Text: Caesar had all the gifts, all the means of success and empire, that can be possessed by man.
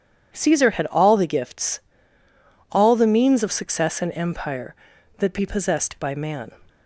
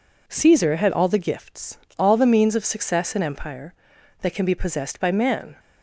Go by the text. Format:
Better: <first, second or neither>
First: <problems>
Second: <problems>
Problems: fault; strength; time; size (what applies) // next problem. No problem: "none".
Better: second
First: skips "can"; at 5.3 s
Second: none